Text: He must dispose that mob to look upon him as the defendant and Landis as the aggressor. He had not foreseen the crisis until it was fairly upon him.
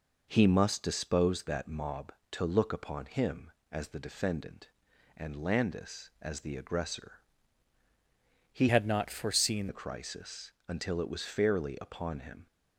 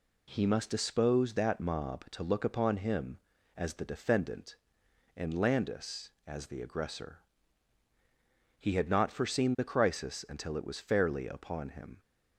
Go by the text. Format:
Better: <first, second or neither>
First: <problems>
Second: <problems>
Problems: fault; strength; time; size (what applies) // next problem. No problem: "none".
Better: second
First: changes voice from "had" to "foreseen"; from 8.6 to 9.6 s; 1.0 s long // pauses between "crisis" and "until"; slight; at 10.5 s; 0.16 s long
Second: none